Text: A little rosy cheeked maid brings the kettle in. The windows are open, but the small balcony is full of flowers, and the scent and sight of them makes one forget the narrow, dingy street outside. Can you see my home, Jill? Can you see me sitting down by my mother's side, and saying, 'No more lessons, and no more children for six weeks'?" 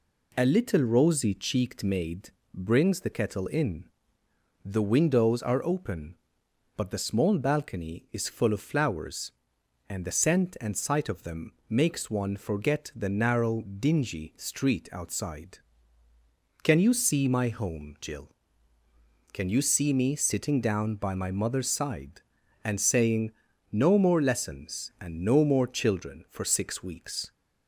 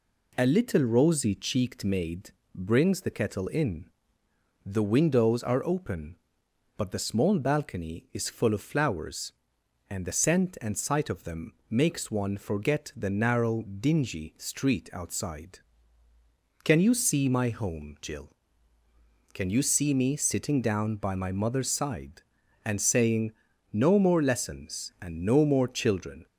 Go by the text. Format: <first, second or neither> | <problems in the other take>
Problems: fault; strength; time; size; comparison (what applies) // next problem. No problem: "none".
first | pauses between "maid" and "brings"; slight; at 2.3 s; 0.24 s long; slight in the first // pauses between "them" and "makes"; slight; at 11.5 s; 0.18 s long; slight in the first // stops before "for six weeks"; at 26.2 s